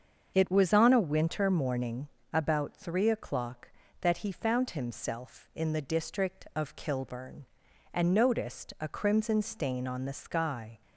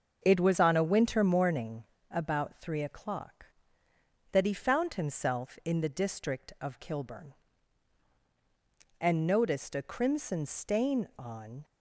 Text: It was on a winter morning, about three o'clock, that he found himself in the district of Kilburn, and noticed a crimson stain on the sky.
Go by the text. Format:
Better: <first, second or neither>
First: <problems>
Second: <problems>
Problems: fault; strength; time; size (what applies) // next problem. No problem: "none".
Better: first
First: starts louder than the rest; until 1.3 s; 6.5 dB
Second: starts louder than the rest; until 1.2 s; 7 dB // stops before "the sky"; at 11.6 s